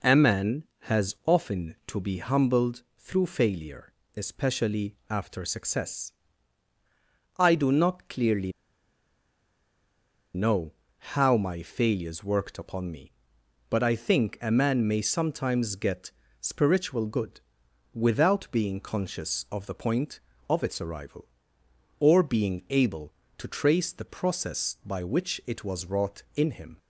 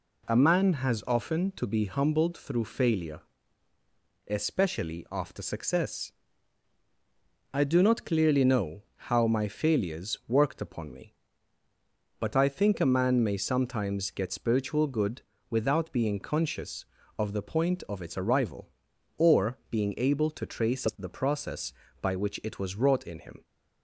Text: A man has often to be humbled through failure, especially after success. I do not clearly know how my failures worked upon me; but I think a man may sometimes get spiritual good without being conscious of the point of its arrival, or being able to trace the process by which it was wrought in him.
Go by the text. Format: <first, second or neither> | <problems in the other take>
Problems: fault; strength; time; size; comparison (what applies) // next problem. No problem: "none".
second | pauses between "clearly" and "know"; strong; at 8.5 s; 1.8 s long // pauses between "know" and "how"; at 10.7 s; 0.40 s long // pauses between "get" and "spiritual"; slight; at 16.1 s; 0.28 s long // pauses between "good" and "without"; noticeable; at 17.3 s; 0.56 s long; slight in the second